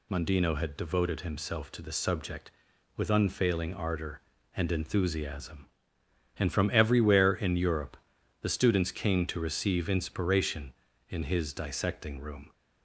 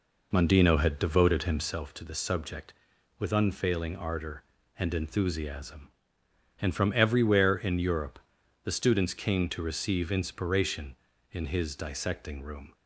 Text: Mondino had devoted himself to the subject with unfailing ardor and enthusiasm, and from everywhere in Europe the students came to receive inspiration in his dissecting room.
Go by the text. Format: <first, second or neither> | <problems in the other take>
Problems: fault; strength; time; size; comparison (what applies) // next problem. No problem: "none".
first | starts louder than the rest; noticeable; until 1.8 s; 4 dB // pauses between "Europe" and "the"; noticeable; at 8.1 s; 0.46 s long; noticeable in the first